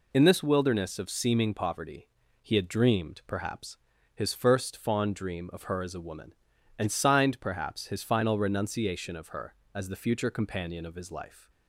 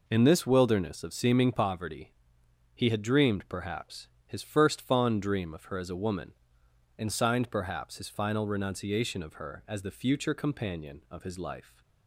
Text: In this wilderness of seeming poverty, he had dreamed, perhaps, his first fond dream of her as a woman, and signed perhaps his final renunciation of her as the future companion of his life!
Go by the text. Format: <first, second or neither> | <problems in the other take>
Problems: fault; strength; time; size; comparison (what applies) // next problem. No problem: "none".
neither | none